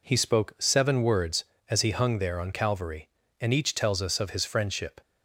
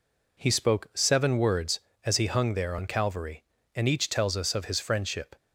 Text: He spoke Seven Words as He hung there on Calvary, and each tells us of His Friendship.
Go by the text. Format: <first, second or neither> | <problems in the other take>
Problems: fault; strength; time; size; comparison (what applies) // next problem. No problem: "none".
neither | none